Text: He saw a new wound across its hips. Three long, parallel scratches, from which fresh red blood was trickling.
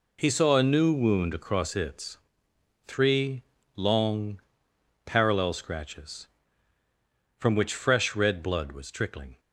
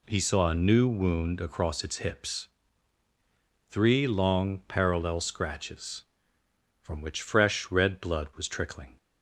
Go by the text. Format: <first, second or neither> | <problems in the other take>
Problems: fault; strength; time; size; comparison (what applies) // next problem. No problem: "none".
second | skips "hips"; at 2.5 s // pauses between "Three" and "long"; slight; at 3.4 s; 0.36 s long